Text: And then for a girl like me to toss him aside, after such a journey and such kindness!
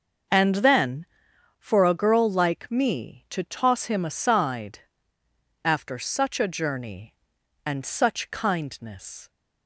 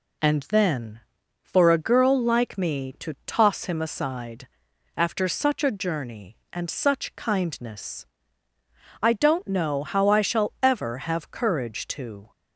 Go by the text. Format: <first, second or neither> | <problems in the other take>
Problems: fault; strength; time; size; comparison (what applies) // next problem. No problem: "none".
first | goes on to say "I don't know how I shall ever have courage to"; strong; from 9.0 s on; 3.3 s long